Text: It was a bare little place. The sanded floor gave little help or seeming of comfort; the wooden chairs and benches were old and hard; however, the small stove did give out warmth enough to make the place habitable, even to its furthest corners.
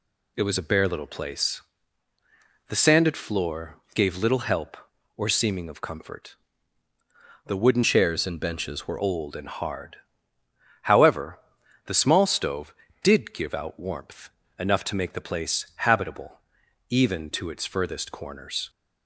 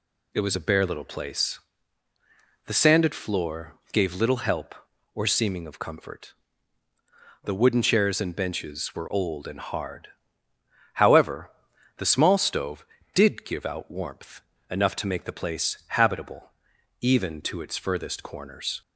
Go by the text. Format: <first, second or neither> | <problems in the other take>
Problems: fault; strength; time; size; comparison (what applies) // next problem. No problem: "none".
second | pauses between "floor" and "gave"; slight; at 3.7 s; 0.18 s long; slight in the second // changes voice from "chairs" to "were"; from 7.8 to 8.9 s; 1.1 s long // pauses between "warmth" and "enough"; slight; at 14.2 s; 0.30 s long; slight in the second